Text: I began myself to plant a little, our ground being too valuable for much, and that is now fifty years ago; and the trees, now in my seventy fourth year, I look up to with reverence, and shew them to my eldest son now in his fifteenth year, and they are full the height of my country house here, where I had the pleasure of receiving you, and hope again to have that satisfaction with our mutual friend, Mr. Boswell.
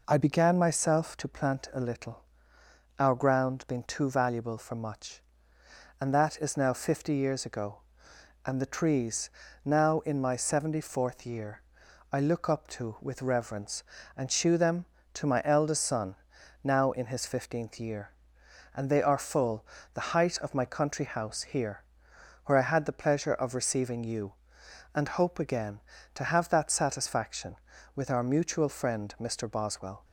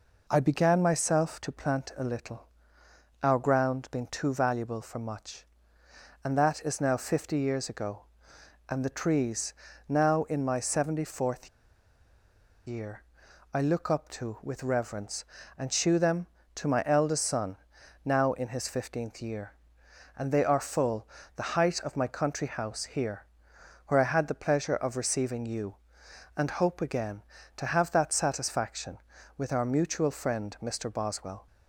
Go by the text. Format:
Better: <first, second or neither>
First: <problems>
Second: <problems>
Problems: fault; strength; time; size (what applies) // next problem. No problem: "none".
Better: first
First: pauses between "son" and "now"; noticeable; at 16.1 s; 0.50 s long // pauses between "full" and "the"; slight; at 19.6 s; 0.30 s long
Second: pauses between "fourth" and "year"; at 11.4 s; 1.1 s long // pauses between "son" and "now"; noticeable; at 17.5 s; 0.50 s long // pauses between "full" and "the"; slight; at 21.0 s; 0.30 s long